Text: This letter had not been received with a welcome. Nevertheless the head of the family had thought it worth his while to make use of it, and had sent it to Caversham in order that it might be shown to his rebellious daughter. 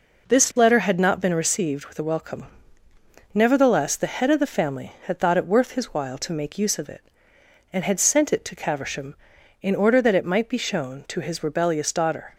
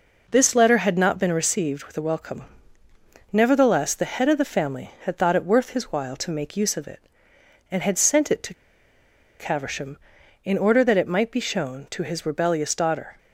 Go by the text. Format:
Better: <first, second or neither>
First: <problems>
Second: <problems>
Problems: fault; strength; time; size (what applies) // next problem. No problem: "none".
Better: first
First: none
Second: pauses between "to" and "Caversham"; noticeable; at 8.5 s; 0.86 s long